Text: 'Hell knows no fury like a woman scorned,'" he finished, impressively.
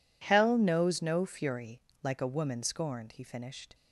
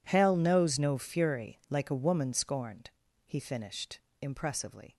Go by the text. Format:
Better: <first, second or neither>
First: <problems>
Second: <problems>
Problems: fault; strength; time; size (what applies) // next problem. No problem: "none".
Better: second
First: pauses between "fury" and "like"; slight; at 1.8 s; 0.24 s long // stops before "impressively"; at 3.7 s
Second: none